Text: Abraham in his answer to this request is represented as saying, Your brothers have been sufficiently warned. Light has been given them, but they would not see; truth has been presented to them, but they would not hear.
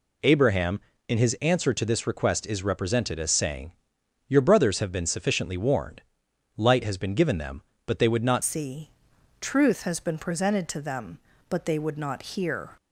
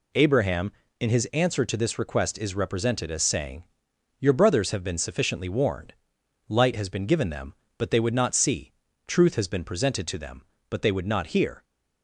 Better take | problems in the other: second | changes voice at "see"; from 8.4 s on; 4.3 s long

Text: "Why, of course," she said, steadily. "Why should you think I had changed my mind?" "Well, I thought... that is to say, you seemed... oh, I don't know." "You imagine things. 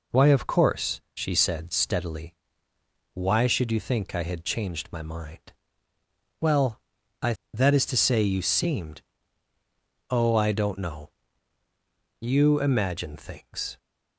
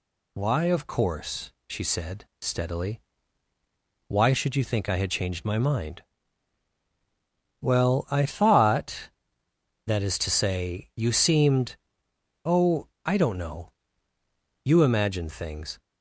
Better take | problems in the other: second | skips "thought"; at 7.4 s

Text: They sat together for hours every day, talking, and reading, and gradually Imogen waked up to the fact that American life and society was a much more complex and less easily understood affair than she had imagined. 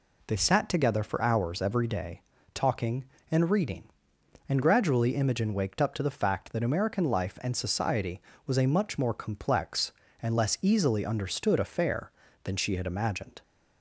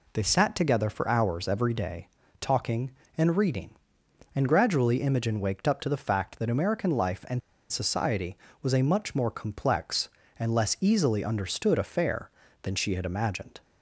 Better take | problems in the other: first | pauses between "and" and "society"; slight; at 7.4 s; 0.30 s long

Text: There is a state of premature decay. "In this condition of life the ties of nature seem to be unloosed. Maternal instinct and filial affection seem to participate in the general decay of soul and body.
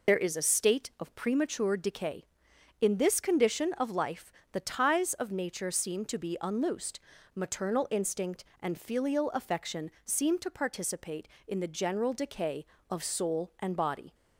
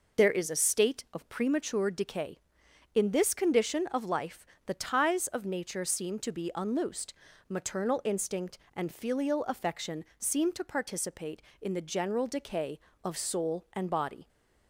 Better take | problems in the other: second | loses the start of "There"; at 0.0 s; 55 ms // pauses between "life" and "the"; slight; at 4.3 s; 0.22 s long; slight in the second

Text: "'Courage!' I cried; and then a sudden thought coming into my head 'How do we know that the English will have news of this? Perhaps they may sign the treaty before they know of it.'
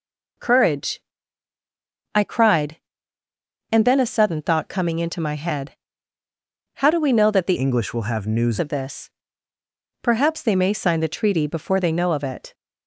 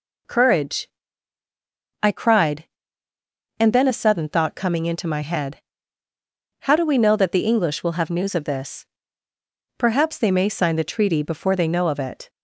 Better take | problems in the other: second | pauses between "head" and "How"; at 5.7 s; 1.0 s long; also in the second // changes voice from "English" to "news"; from 7.5 to 8.5 s; 1.0 s long

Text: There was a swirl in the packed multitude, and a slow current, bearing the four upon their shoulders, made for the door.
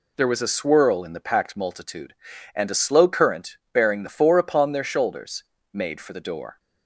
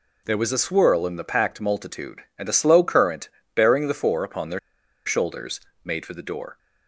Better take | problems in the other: first | pauses between "their" and "shoulders"; noticeable; at 4.5 s; 0.46 s long

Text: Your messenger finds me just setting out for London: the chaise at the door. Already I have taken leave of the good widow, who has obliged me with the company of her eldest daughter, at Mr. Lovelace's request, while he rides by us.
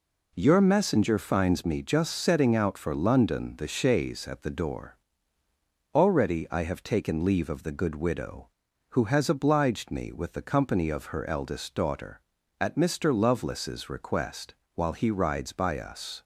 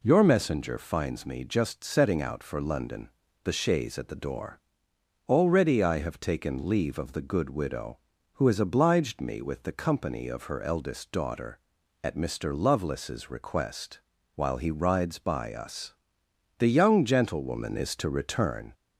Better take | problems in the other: first | goes on to say "The young gentlewoman is to return"; strong; from 16.5 s on; 2.1 s long

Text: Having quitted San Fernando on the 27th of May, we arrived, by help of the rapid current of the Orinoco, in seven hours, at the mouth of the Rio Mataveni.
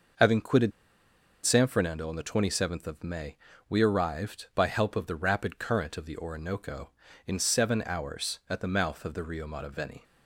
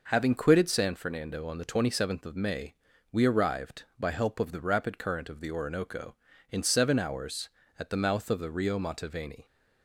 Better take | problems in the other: second | pauses between "quitted" and "San"; noticeable; at 0.7 s; 0.76 s long

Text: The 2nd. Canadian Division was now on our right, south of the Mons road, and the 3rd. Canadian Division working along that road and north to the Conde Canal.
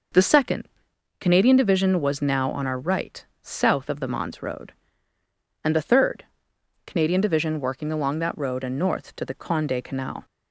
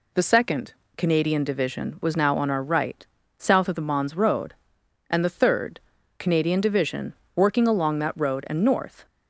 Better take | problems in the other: first | pauses between "Division" and "working"; slight; at 7.1 s; 0.20 s long // stops before "to the Conde Canal"; at 9.0 s

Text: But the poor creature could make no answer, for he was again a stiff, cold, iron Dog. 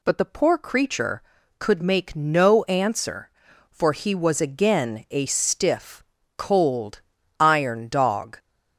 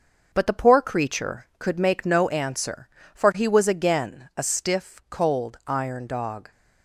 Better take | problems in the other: first | gets quieter; noticeable; throughout; 4 dB

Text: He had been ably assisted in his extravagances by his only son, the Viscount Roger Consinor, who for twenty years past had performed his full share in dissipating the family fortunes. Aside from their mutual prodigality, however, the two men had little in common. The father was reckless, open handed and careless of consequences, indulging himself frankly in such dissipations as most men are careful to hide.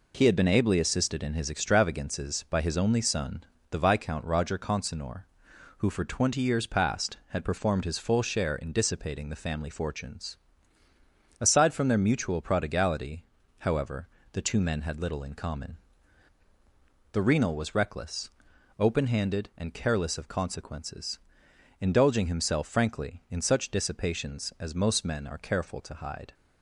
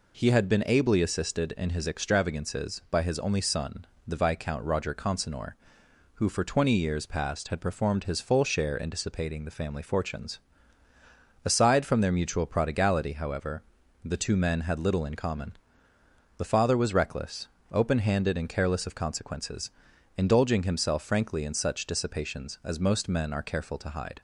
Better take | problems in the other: second | says "renal" for "father"; at 17.2 s

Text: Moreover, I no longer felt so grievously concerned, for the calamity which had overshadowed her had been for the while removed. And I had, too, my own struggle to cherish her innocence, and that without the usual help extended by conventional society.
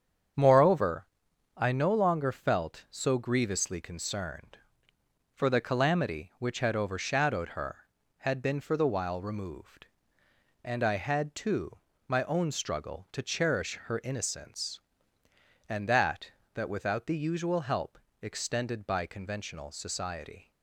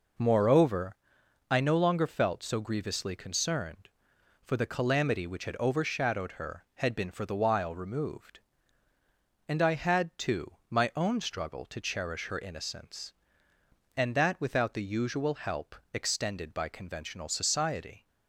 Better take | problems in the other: second | starts louder than the rest; strong; until 1.8 s; 8 dB // says "that" twice; at 16.5 s // pauses between "help" and "extended"; slight; at 17.9 s; 0.24 s long; slight in the second

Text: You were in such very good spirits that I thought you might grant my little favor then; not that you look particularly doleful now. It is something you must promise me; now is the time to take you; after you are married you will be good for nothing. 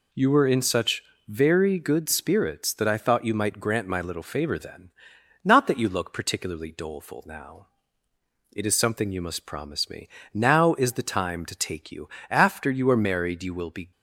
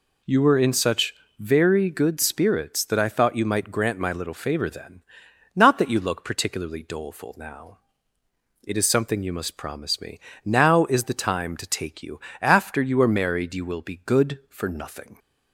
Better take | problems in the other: second | pauses between "such" and "very"; slight; at 1.0 s; 0.24 s long; slight in the second // stops before "good for nothing"; at 13.9 s

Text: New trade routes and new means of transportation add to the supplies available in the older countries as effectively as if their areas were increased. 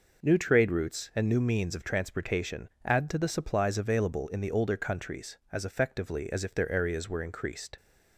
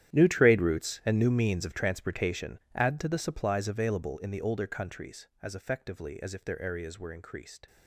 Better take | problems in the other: first | gets quieter; strong; throughout; 16.5 dB // pauses between "transportation" and "add"; slight; at 2.6 s; 0.16 s long; slight in the first

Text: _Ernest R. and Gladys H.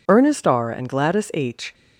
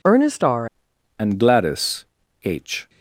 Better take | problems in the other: first | changes voice at "and"; from 1.1 s on; 1.7 s long // pauses between "Gladys" and "H"; at 2.0 s; 0.40 s long

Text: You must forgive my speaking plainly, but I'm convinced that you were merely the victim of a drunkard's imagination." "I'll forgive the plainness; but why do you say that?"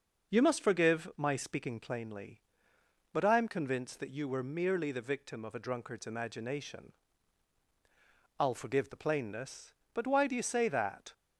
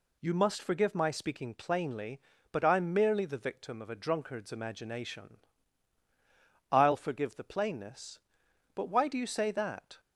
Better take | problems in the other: first | skips "convinced that you were"; at 2.9 s

